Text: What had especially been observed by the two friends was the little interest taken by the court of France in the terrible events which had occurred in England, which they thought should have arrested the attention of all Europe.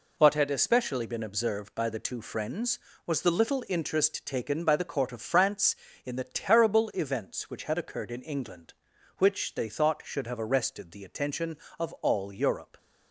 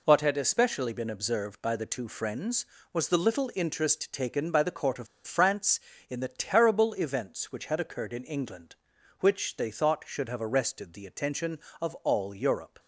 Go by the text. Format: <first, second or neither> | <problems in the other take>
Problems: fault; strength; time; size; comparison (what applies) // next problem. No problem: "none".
first | pauses between "of" and "France"; slight; at 5.0 s; 0.20 s long